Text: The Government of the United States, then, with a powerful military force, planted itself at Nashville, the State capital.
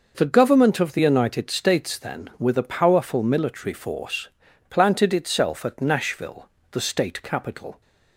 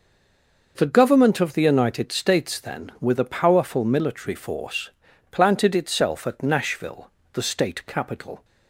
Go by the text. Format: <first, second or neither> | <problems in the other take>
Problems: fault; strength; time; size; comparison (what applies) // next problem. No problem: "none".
first | stays silent before the first word; slight; until 0.7 s; 0.7 s long